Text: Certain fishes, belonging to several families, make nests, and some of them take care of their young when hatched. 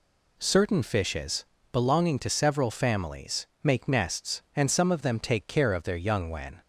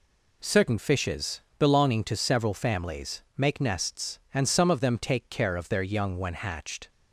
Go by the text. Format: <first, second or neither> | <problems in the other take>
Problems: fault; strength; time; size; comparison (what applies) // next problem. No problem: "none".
second | stops before "hatched"; at 6.6 s